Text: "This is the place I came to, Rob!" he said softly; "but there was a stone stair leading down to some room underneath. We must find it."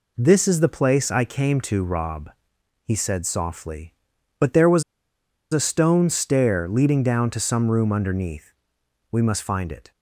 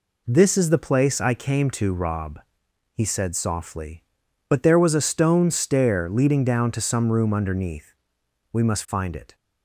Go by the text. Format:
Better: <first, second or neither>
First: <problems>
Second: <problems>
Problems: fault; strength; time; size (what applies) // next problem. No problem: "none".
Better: second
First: pauses between "was" and "a"; noticeable; at 4.8 s; 0.69 s long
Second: none